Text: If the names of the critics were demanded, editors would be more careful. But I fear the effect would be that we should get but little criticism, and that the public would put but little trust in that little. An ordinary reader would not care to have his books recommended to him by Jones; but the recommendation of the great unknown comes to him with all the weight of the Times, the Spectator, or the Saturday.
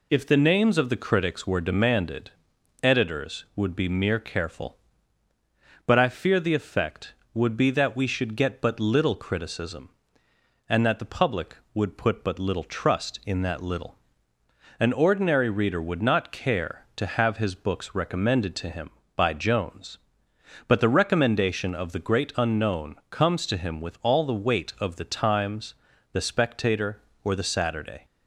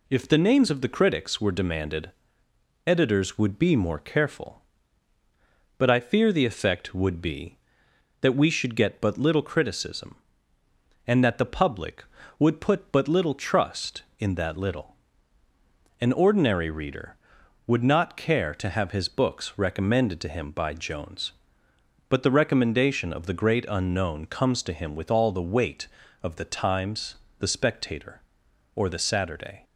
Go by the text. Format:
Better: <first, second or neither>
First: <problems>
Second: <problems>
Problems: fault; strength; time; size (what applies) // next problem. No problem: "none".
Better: second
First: says "mere" for "more"; at 3.8 s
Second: none